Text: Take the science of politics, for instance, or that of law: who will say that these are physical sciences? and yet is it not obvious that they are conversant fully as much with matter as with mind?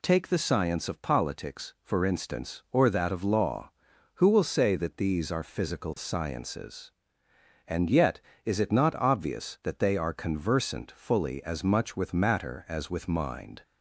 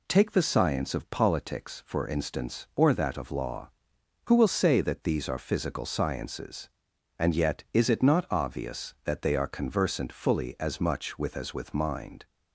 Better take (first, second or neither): first